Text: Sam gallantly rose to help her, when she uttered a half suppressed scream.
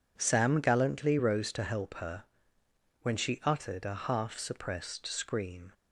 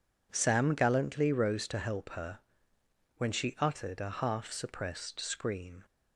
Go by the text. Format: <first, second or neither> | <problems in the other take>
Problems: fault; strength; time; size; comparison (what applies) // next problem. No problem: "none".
neither | none